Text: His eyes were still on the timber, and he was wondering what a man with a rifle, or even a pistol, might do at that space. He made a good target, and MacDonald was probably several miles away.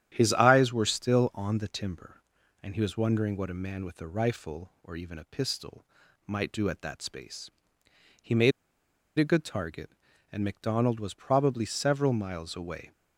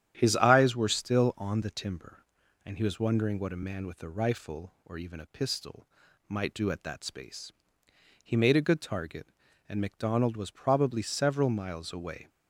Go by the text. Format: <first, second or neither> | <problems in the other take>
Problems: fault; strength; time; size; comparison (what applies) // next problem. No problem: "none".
second | starts louder than the rest; strong; until 1.1 s; 10 dB; strong in the second // pauses between "made" and "a"; noticeable; at 8.5 s; 0.66 s long